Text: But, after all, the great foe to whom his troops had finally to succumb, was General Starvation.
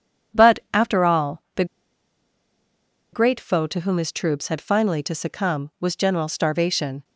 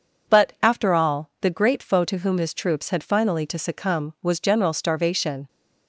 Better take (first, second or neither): second